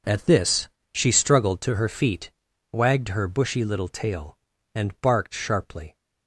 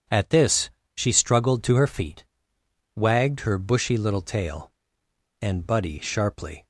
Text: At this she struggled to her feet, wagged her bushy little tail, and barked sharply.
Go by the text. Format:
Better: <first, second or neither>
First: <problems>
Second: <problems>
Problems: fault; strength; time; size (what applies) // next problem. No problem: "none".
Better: first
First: pauses between "this" and "she"; slight; at 0.6 s; 0.24 s long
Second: pauses between "this" and "she"; slight; at 0.6 s; 0.26 s long // says "buddy" for "barked"; at 5.6 s